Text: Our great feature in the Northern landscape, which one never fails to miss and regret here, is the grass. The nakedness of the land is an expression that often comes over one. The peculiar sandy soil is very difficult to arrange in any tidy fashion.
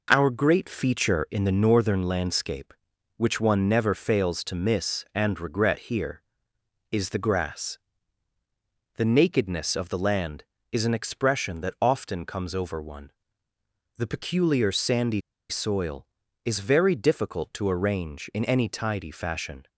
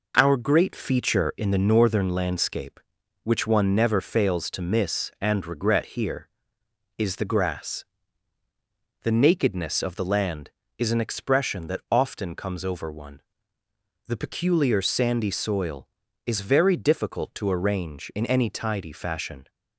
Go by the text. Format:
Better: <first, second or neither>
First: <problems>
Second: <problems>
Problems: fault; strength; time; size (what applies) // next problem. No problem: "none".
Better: second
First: pauses between "sandy" and "soil"; slight; at 15.2 s; 0.28 s long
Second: none